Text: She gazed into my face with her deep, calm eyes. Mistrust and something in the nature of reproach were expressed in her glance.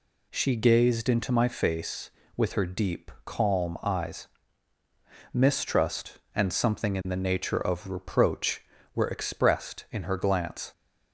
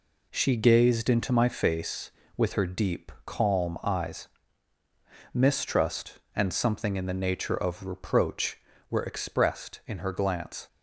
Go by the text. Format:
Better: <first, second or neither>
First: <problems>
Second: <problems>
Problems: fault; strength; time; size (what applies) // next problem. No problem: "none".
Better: first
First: none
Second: gets quieter; throughout; 7 dB